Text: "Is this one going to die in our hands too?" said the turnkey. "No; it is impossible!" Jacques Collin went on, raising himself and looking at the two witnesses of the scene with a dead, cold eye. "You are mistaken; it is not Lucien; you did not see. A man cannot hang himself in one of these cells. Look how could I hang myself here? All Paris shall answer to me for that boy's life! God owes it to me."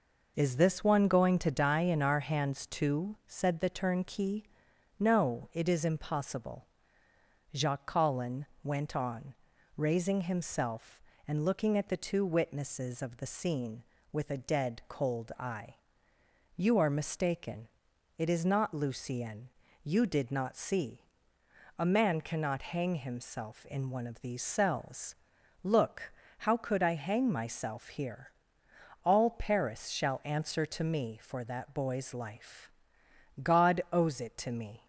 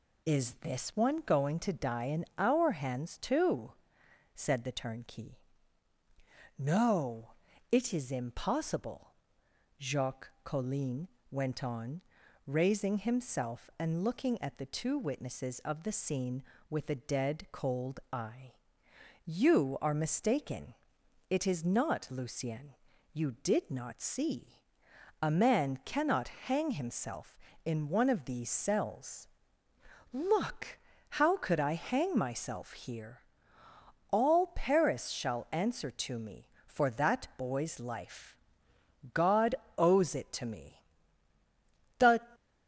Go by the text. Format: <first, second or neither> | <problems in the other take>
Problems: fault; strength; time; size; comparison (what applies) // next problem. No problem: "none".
first | pauses between "Collin" and "went"; slight; at 11.0 s; 0.24 s long; slight in the first // pauses between "Look" and "how"; slight; at 30.7 s; 0.30 s long; slight in the first // pauses between "God" and "owes"; slight; at 39.5 s; 0.24 s long // goes on to say "The"; slight; from 41.9 s on; 0.30 s long